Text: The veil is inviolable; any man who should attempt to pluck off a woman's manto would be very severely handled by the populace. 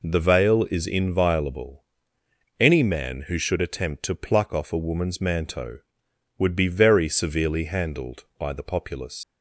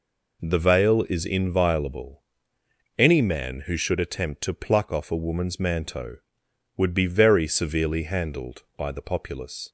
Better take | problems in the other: second | leaves "populace" unfinished; at 9.2 s; 80 ms

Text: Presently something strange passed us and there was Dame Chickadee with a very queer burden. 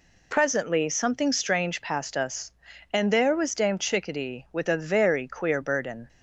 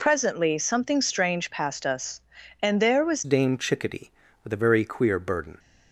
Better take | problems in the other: first | changes voice at "Dame"; from 3.2 s on; 2.3 s long

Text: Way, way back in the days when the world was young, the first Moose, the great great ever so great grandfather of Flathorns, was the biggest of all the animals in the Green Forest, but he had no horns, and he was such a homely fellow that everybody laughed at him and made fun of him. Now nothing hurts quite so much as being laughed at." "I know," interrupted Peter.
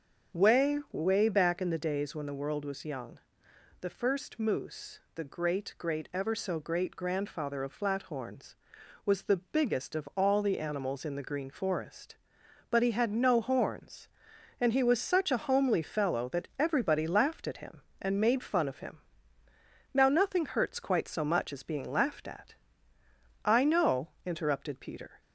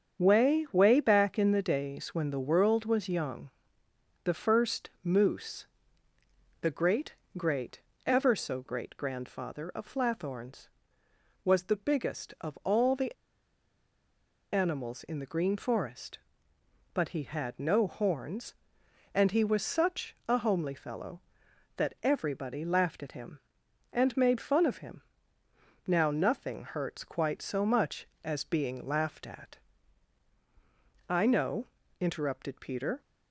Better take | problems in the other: first | starts louder than the rest; strong; until 1.2 s; 7.5 dB; strong in the first // pauses between "great" and "great"; slight; at 7.1 s; 0.22 s long // pauses between "great" and "ever"; slight; at 7.7 s; 0.26 s long // pauses between "the" and "animals"; strong; at 13.1 s; 1.3 s long

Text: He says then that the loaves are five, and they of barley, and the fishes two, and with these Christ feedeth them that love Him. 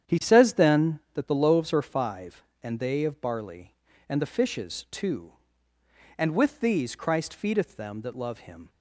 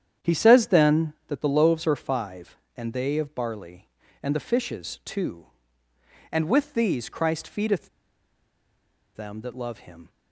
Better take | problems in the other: first | starts louder than the rest; strong; until 1.3 s; 9 dB; strong in the first // pauses between "feedeth" and "them"; strong; at 7.8 s; 1.2 s long

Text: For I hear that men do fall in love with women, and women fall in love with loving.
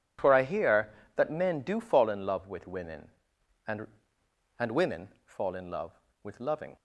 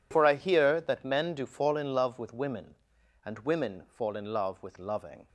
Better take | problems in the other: second | says "and" twice; at 4.5 s // pauses between "women" and "fall"; slight; at 5.0 s; 0.16 s long

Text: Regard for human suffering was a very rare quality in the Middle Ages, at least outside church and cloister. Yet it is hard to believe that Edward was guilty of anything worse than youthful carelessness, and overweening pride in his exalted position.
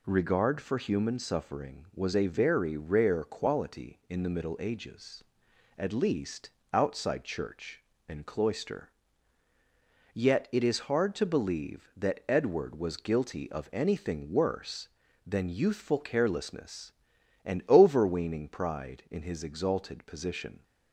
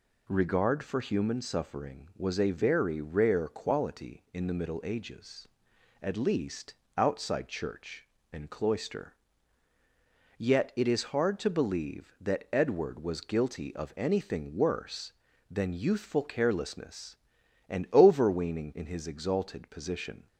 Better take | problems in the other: first | pauses between "least" and "outside"; slight; at 6.7 s; 0.24 s long; slight in the first // skips "pride"; at 18.7 s

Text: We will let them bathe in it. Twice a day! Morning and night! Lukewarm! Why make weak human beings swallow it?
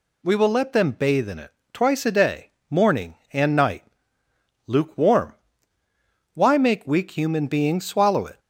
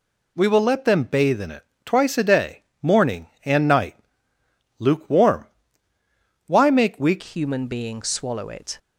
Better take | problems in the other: first | changes voice at "human"; from 7.2 s on; 1.5 s long

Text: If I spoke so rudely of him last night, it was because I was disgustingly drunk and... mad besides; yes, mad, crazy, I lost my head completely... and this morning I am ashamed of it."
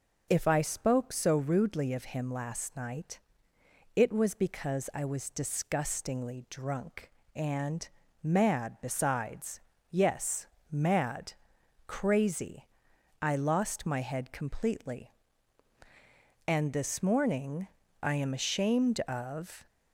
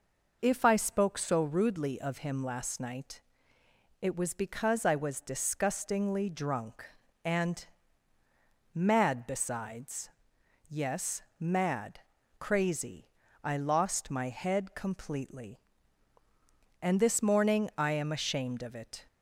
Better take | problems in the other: second | pauses between "morning" and "I"; slight; at 17.6 s; 0.34 s long // stops before "it"; at 19.6 s

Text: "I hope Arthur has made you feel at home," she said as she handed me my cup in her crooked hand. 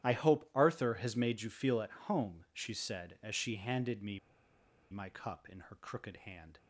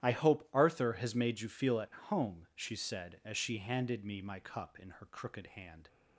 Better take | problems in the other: second | starts louder than the rest; strong; until 1.0 s; 11.5 dB; strong in the second // pauses between "me" and "my"; noticeable; at 4.1 s; 0.73 s long

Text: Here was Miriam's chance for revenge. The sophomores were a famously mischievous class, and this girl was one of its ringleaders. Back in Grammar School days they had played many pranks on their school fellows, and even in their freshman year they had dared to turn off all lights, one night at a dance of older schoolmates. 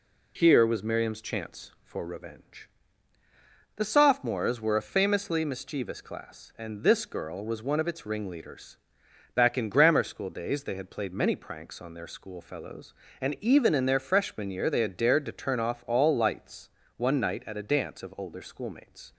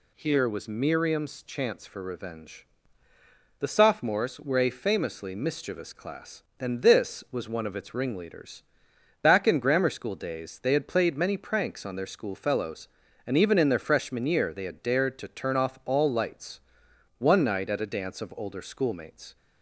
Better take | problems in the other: first | skips "girl"; at 7.2 s

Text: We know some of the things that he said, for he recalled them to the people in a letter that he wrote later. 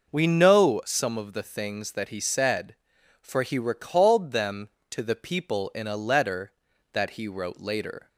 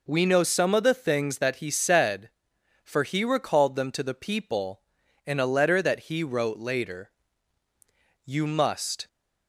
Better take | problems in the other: first | goes on to say "You must"; noticeable; from 8.2 s on; 0.82 s long

